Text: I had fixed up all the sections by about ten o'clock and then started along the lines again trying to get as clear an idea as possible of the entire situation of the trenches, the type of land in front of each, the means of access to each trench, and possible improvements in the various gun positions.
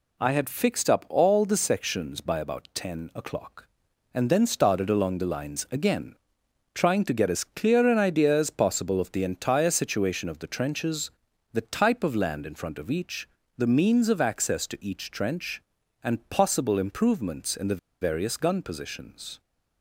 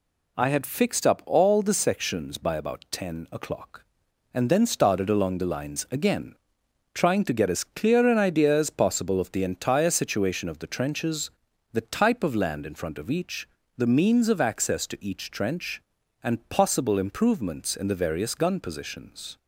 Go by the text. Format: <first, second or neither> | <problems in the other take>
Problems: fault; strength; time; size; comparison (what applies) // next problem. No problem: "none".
second | pauses between "again" and "trying"; noticeable; at 6.1 s; 0.60 s long; noticeable in the second // pauses between "the" and "various"; slight; at 17.7 s; 0.24 s long